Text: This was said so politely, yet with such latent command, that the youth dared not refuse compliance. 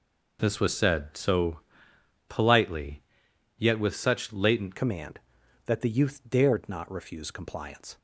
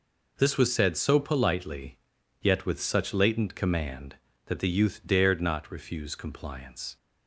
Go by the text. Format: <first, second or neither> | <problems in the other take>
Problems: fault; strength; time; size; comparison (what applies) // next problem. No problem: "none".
second | pauses between "so" and "politely"; noticeable; at 1.6 s; 0.68 s long // changes voice at "command"; from 4.7 s on; 3.2 s long